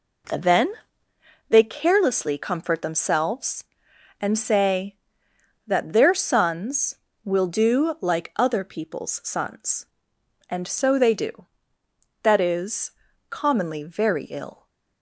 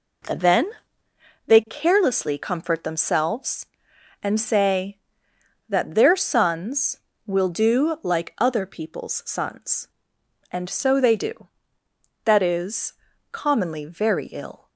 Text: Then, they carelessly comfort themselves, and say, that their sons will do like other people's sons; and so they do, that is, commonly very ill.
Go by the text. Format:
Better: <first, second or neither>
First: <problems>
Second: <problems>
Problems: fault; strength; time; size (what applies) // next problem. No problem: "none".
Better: neither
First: none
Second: none